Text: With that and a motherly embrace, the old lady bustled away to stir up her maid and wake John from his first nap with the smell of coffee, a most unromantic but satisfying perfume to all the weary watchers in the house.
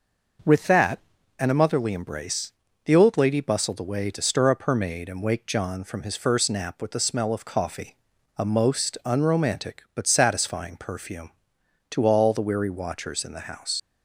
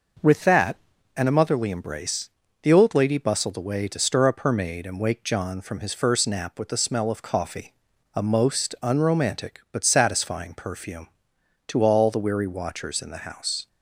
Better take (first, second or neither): second